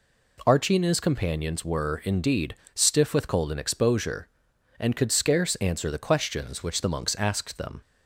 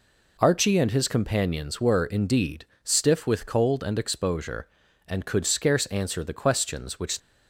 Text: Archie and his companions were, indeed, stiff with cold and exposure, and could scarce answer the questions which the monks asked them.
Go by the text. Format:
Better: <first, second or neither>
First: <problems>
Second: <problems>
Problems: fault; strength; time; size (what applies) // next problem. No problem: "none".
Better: first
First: none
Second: stops before "the monks asked them"; at 7.1 s